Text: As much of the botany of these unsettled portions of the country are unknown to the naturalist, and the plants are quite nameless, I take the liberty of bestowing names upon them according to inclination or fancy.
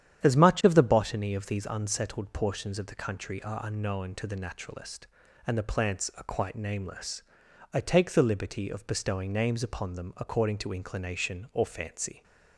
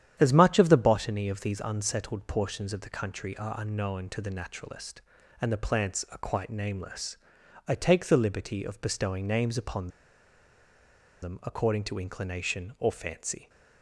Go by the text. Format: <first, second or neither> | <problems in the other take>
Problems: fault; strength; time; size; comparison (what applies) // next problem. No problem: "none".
first | starts louder than the rest; strong; until 1.2 s; 10 dB; strong in the first // pauses between "upon" and "them"; strong; at 9.8 s; 1.3 s long